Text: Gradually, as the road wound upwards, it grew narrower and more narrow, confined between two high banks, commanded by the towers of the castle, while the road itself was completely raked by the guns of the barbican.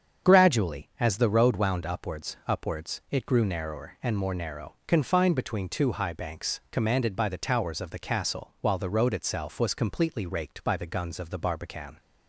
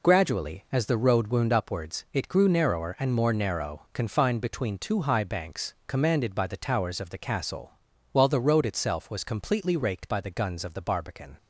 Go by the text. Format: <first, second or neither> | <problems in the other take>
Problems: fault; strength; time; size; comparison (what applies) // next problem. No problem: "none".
second | starts louder than the rest; strong; until 1.4 s; 7.5 dB // says "upwards" twice; at 2.4 s